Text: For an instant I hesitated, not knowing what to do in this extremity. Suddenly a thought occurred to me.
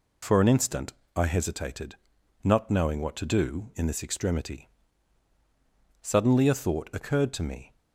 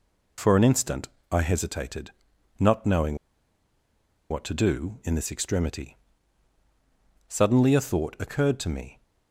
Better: first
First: pauses between "instant" and "I"; slight; at 0.9 s; 0.24 s long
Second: pauses between "instant" and "I"; slight; at 1.0 s; 0.24 s long // pauses between "knowing" and "what"; at 3.1 s; 1.1 s long

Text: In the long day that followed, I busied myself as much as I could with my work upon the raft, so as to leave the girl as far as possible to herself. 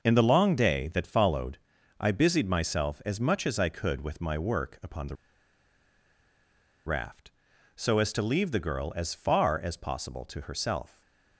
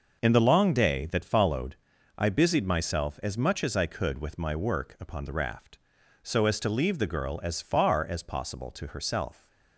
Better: second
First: pauses between "the" and "raft"; strong; at 5.1 s; 1.7 s long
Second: none

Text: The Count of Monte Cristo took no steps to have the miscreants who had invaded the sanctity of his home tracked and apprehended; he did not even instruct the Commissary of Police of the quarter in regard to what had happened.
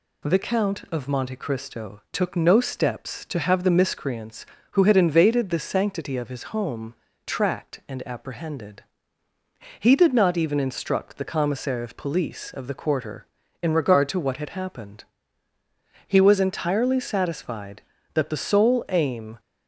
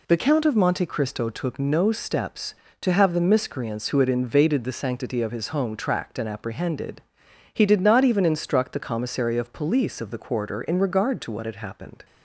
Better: second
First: pauses between "home" and "tracked"; slight; at 6.9 s; 0.32 s long // goes on to say "He was entirely satisfied that the sole aim"; strong; from 16.0 s on; 3.3 s long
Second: none

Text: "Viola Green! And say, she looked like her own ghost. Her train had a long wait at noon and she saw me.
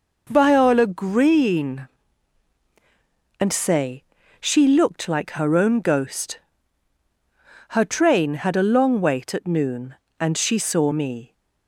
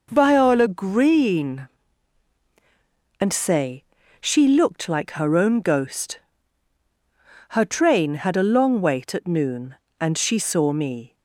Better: neither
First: none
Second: none

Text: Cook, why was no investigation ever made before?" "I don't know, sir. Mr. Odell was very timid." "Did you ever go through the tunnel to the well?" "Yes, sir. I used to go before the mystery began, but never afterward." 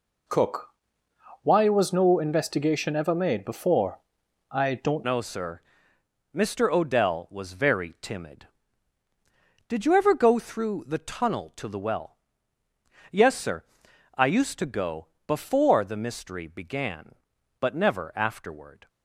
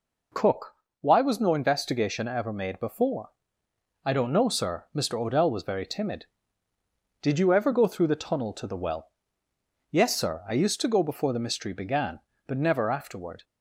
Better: second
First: changes voice at "know"; from 5.0 s on; 13.8 s long // pauses between "go" and "before"; slight; at 15.0 s; 0.22 s long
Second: none

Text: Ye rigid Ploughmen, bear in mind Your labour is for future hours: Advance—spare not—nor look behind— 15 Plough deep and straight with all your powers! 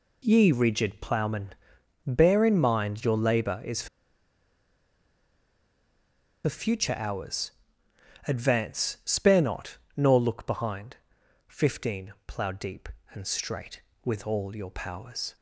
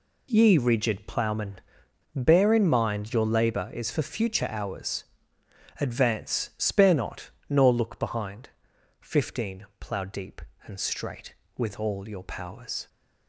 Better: second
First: pauses between "for" and "future"; strong; at 3.8 s; 2.5 s long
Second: none

